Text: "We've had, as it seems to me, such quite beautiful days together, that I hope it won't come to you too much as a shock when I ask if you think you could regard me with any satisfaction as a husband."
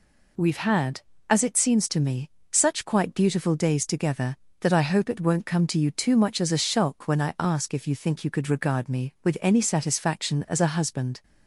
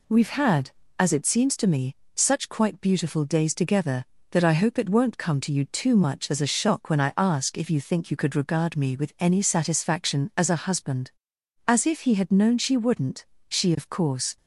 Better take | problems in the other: first | goes on to say "As if he had known she wouldn't she of course"; strong; from 11.6 s on; 2.6 s long

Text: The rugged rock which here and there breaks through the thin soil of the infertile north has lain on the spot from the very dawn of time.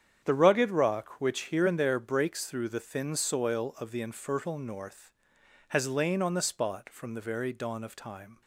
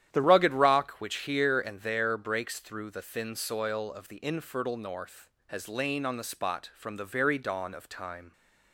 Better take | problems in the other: first | starts louder than the rest; strong; until 1.1 s; 10.5 dB; strong in the first // changes voice at "rugged"; from 0.2 s on; 8.1 s long

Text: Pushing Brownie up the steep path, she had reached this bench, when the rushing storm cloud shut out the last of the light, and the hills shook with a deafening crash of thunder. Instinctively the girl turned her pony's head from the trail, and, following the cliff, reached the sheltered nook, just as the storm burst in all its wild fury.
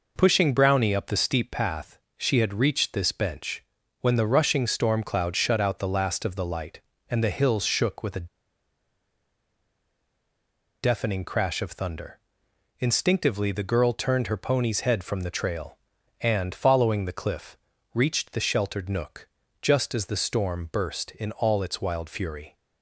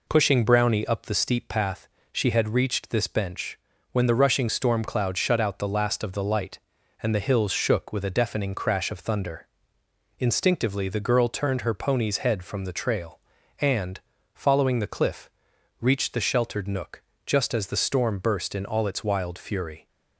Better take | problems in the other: second | pauses between "a" and "deafening"; strong; at 8.2 s; 2.5 s long

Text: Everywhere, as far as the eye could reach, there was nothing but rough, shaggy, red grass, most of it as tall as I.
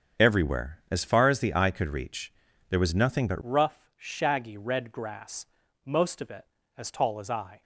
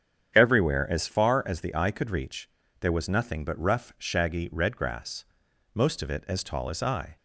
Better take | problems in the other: second | starts louder than the rest; strong; until 1.3 s; 7.5 dB; strong in the second // changes voice at "rough"; from 3.4 s on; 4.2 s long

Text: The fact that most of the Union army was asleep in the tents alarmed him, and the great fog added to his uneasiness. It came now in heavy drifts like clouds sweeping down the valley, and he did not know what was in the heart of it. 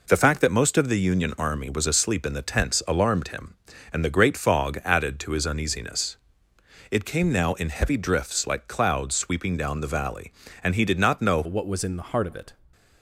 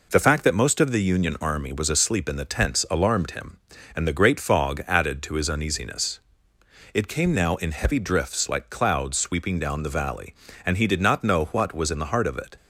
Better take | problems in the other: second | changes voice at "what"; from 11.4 s on; 1.1 s long

